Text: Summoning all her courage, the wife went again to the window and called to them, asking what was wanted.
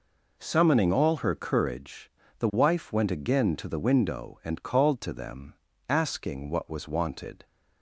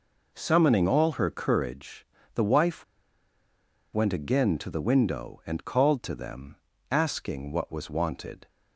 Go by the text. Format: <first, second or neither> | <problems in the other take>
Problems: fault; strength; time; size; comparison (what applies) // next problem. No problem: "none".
first | pauses between "wife" and "went"; at 2.8 s; 1.0 s long